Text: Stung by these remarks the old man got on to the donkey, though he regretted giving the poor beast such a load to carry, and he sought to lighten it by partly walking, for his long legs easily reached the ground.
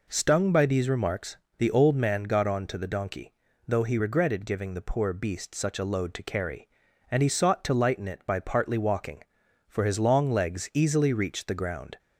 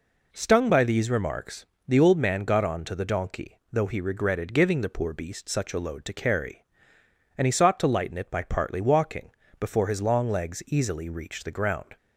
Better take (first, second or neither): first